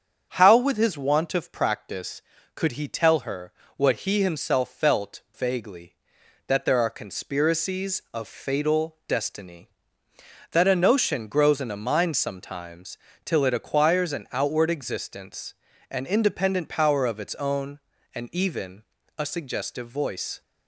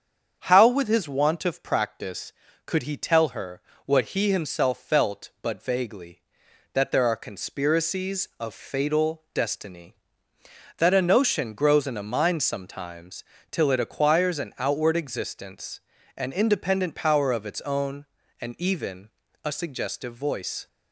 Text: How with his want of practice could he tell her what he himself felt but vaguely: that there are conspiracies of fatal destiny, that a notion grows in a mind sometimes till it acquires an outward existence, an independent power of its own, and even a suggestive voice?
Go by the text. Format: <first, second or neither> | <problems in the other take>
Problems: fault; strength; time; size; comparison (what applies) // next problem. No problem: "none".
second | starts louder than the rest; strong; until 1.3 s; 7.5 dB; strong in the second // pauses between "her" and "what"; slight; at 3.5 s; 0.24 s long; slight in the second // skips "but"; at 5.2 s // pauses between "sometimes" and "till"; slight; at 12.9 s; 0.26 s long; slight in the second // pauses between "even" and "a"; slight; at 18.8 s; 0.34 s long; slight in the second